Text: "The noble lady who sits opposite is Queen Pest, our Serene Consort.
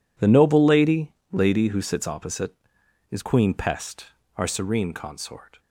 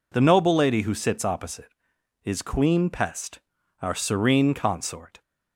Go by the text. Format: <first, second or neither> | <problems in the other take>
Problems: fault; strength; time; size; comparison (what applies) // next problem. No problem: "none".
second | says "lady" twice; at 1.3 s